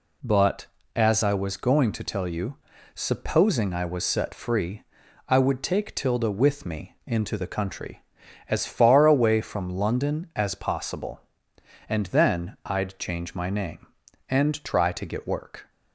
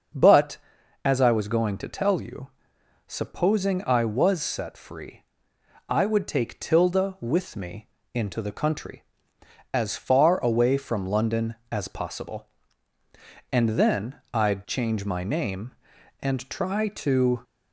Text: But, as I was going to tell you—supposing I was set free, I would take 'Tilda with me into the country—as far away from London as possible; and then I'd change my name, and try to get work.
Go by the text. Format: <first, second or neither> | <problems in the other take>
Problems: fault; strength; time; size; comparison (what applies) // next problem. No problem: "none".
first | starts louder than the rest; until 1.6 s; 6 dB // pauses between "me" and "into"; slight; at 7.8 s; 0.26 s long // stops before "get work"; at 17.4 s